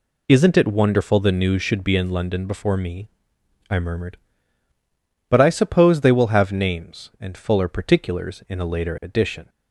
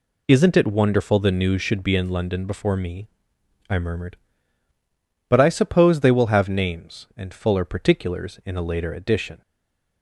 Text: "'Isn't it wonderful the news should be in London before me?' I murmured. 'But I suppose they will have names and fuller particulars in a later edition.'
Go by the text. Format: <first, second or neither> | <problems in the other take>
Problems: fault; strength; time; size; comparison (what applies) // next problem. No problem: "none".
first | stays silent after the last word; slight; from 9.4 s on; 0.6 s long